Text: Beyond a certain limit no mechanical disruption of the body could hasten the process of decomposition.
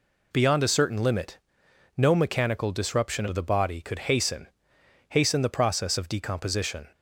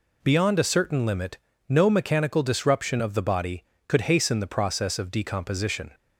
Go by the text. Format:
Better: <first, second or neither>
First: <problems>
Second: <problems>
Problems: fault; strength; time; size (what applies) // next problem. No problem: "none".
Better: second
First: pauses between "limit" and "no"; noticeable; at 1.3 s; 0.58 s long // says "hasten" twice; at 5.0 s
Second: pauses between "limit" and "no"; slight; at 1.3 s; 0.28 s long